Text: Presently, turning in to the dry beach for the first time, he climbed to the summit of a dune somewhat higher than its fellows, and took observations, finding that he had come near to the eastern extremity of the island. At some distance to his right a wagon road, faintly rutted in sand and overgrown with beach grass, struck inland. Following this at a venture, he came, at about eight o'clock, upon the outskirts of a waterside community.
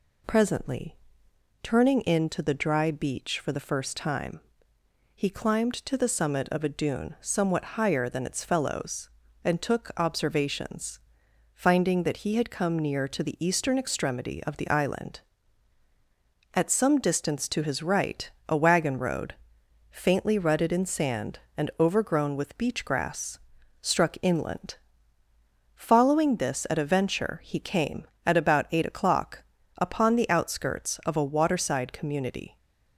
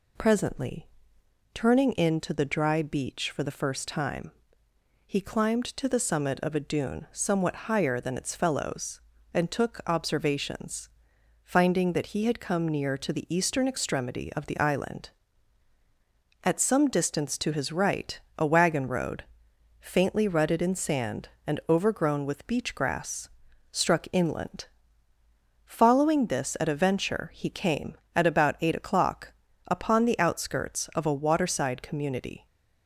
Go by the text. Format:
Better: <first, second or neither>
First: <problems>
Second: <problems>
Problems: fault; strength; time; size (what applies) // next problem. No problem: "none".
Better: neither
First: pauses between "right" and "a"; slight; at 18.2 s; 0.20 s long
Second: pauses between "right" and "a"; slight; at 18.1 s; 0.20 s long